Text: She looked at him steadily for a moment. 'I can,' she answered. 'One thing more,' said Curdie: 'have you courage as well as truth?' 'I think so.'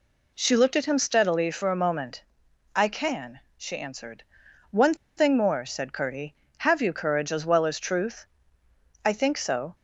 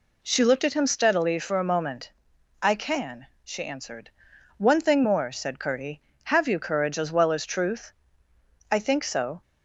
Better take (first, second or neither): second